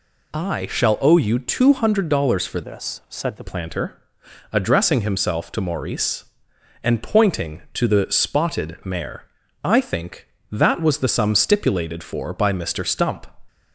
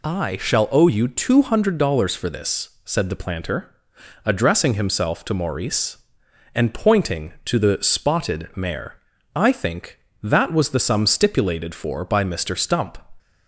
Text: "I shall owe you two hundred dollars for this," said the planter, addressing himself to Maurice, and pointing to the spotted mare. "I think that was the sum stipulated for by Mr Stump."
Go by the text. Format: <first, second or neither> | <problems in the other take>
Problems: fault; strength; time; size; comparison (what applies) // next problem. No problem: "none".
second | changes voice from "this" to "the"; from 2.6 to 3.4 s; 0.8 s long